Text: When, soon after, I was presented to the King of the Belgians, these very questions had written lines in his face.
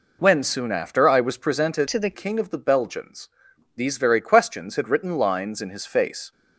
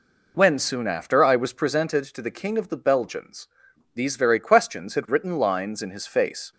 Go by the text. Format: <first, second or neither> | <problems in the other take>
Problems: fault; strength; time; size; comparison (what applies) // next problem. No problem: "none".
second | changes voice from "to" to "the"; from 1.8 to 2.1 s; 0.3 s long